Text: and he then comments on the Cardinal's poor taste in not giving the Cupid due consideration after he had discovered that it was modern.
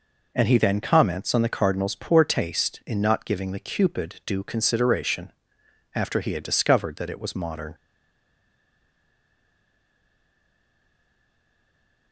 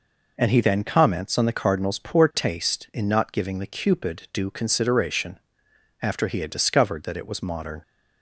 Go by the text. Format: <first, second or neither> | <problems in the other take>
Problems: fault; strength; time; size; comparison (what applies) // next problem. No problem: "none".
second | pauses between "consideration" and "after"; noticeable; at 5.3 s; 0.64 s long; noticeable in the second // stays silent after the last word; strong; from 7.7 s on; 4.4 s long